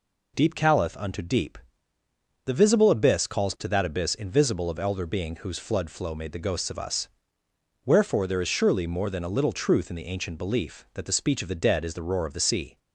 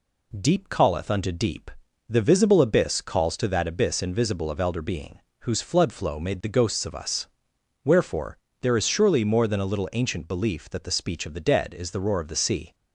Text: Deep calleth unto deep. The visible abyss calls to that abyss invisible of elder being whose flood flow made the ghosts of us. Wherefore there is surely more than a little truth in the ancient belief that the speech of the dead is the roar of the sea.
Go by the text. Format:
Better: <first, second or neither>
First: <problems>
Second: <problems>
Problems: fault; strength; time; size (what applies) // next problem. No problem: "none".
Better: first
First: none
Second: pauses between "being" and "whose"; slight; at 5.1 s; 0.20 s long // pauses between "Wherefore" and "there"; slight; at 8.3 s; 0.24 s long // skips "truth in the"; at 9.9 s